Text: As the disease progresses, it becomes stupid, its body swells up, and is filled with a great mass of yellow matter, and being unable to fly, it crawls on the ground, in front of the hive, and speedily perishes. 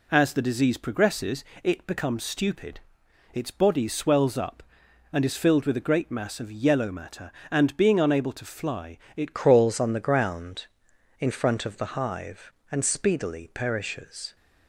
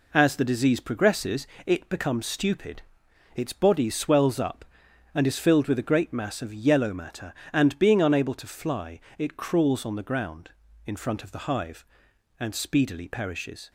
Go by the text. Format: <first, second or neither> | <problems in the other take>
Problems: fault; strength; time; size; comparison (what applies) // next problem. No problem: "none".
second | changes voice at "crawls"; from 9.3 s on; 5.0 s long